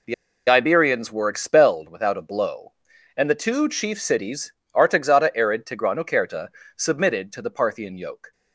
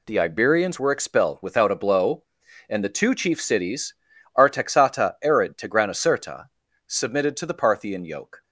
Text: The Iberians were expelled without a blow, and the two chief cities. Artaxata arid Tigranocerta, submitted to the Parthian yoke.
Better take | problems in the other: second | pauses between "The" and "Iberians"; slight; at 0.1 s; 0.35 s long

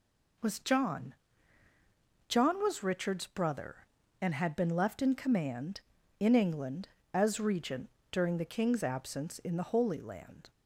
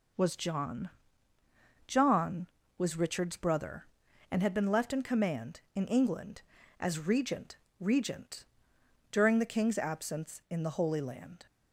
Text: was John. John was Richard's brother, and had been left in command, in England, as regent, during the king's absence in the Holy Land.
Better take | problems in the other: first | says "regent" twice; at 7.7 s

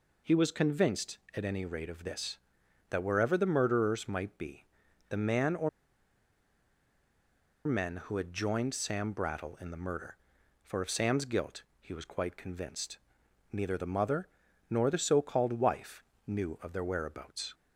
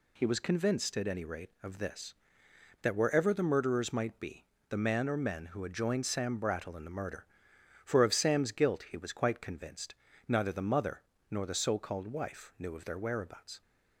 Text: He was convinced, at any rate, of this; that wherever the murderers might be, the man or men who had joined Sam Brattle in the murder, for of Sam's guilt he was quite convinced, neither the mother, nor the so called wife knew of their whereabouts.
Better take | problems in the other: second | pauses between "or" and "men"; strong; at 5.6 s; 1.9 s long // pauses between "guilt" and "he"; slight; at 11.6 s; 0.18 s long // pauses between "wife" and "knew"; slight; at 16.0 s; 0.24 s long

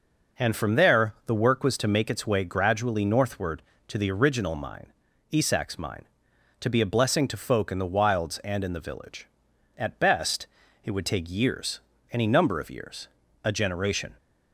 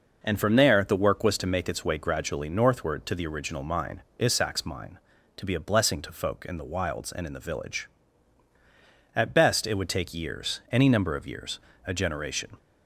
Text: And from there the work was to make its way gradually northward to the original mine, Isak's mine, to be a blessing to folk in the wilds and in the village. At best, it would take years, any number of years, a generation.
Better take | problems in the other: neither | none

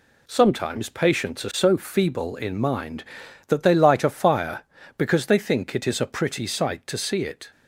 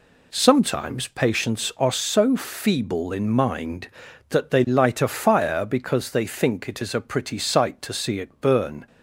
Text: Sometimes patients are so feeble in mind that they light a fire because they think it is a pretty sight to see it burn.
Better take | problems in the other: second | stops before "burn"; at 7.5 s

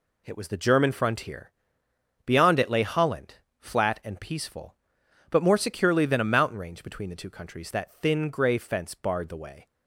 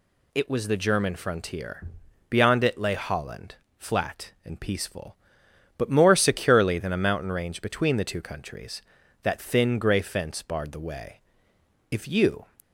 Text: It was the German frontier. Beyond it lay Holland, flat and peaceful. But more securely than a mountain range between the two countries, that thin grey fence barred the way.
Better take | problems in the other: first | goes on to say "If you"; from 11.9 s on; 0.54 s long

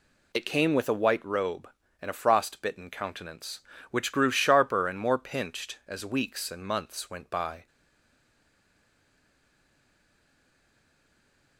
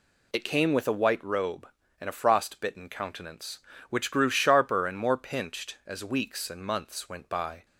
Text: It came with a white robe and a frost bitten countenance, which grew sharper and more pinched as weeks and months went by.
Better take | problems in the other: second | stays silent after the last word; strong; from 7.6 s on; 3.9 s long

